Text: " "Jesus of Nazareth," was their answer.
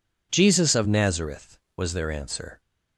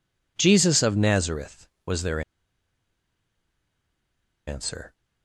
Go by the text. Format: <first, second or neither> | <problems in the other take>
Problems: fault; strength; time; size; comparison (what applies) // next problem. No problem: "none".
first | pauses between "their" and "answer"; strong; at 2.1 s; 2.2 s long